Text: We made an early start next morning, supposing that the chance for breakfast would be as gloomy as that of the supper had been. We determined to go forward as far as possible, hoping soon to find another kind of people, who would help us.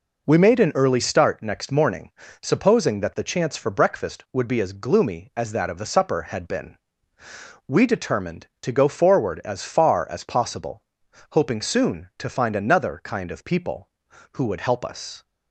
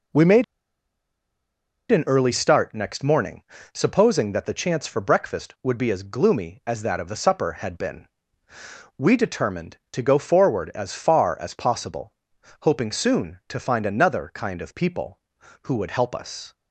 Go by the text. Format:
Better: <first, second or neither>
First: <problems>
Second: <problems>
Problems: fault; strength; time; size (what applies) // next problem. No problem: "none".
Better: first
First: none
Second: pauses between "made" and "an"; strong; at 0.4 s; 1.4 s long